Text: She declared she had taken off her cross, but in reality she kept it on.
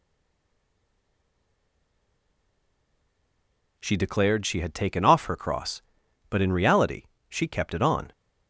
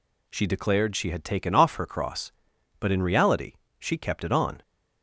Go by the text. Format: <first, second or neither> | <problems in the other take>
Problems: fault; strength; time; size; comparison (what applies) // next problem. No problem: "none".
second | stays silent before the first word; strong; until 3.7 s; 3.7 s long // pauses between "reality" and "she"; slight; at 7.0 s; 0.26 s long; slight in the second